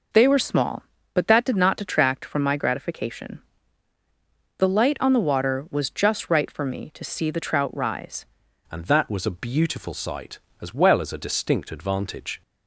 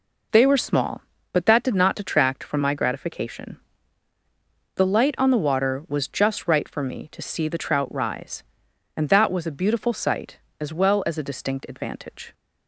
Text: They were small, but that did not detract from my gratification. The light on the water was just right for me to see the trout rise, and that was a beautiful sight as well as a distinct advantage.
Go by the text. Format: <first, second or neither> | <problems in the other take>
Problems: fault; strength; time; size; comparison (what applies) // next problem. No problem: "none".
second | changes voice at "and"; from 8.6 s on; 3.8 s long